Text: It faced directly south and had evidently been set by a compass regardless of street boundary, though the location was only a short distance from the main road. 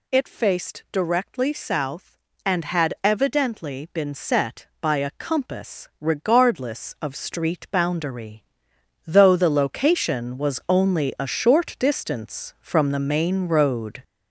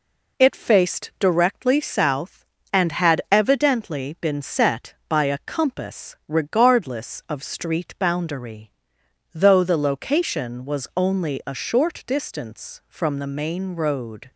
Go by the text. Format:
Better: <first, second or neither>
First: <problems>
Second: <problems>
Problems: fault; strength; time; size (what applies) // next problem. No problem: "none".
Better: second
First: gets louder; throughout; 6 dB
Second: none